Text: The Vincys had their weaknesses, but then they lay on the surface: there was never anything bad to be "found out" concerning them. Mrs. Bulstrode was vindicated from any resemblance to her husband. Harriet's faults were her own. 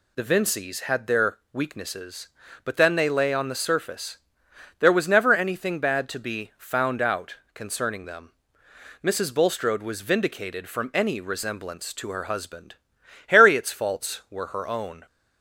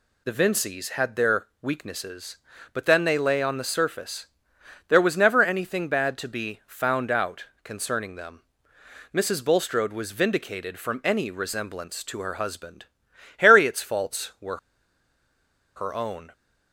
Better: first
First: pauses between "their" and "weaknesses"; slight; at 1.3 s; 0.16 s long // pauses between "out" and "concerning"; slight; at 7.3 s; 0.18 s long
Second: pauses between "their" and "weaknesses"; slight; at 1.4 s; 0.16 s long // pauses between "out" and "concerning"; slight; at 7.4 s; 0.18 s long // pauses between "were" and "her"; at 14.5 s; 1.1 s long

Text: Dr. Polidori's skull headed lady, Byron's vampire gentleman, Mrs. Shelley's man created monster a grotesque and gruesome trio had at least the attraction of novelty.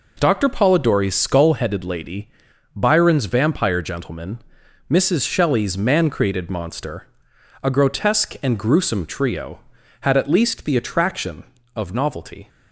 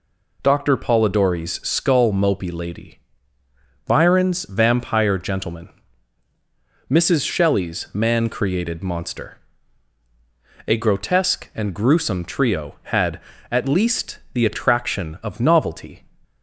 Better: first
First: pauses between "monster" and "a"; noticeable; at 7.0 s; 0.56 s long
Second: says "mopey" for "headed"; at 2.1 s // pauses between "monster" and "a"; strong; at 9.3 s; 1.3 s long

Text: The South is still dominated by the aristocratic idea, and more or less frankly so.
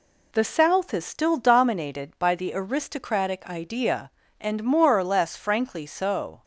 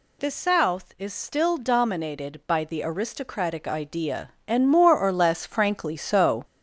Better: first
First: none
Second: gets louder; noticeable; throughout; 5.5 dB

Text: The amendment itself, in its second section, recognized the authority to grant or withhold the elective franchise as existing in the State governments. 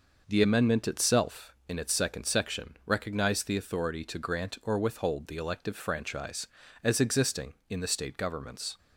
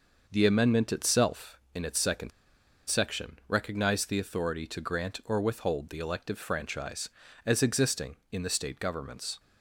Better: first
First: none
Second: pauses between "second" and "section"; noticeable; at 2.3 s; 0.58 s long

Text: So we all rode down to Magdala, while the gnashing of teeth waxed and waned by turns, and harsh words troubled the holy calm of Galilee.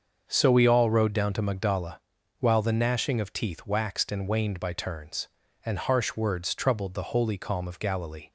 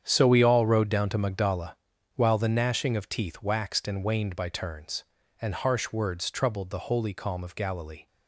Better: first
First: starts louder than the rest; until 1.2 s; 6.5 dB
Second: gets quieter; strong; throughout; 12 dB // starts louder than the rest; strong; until 1.0 s; 8.5 dB

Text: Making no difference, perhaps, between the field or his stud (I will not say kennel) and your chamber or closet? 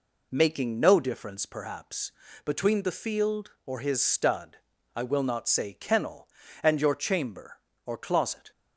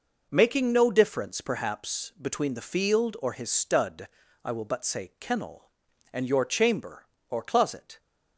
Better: first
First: none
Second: says "but" for "not"; at 4.6 s

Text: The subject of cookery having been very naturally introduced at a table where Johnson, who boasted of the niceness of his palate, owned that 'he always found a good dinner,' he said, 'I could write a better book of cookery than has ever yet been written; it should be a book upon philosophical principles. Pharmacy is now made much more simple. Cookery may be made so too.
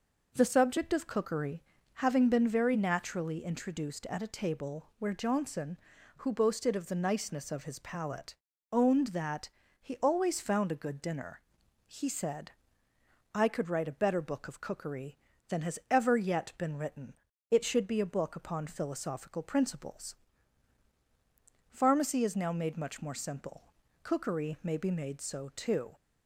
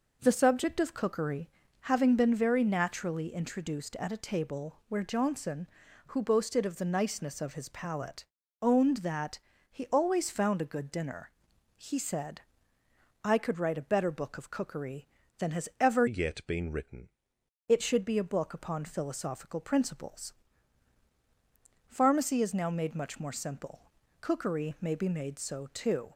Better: first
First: pauses between "cookery" and "having"; slight; at 1.6 s; 0.34 s long // pauses between "that" and "he"; slight; at 9.4 s; 0.32 s long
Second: pauses between "cookery" and "having"; slight; at 1.4 s; 0.34 s long // pauses between "that" and "he"; slight; at 9.3 s; 0.32 s long // changes voice from "yet" to "written"; from 16.0 to 17.0 s; 1.0 s long

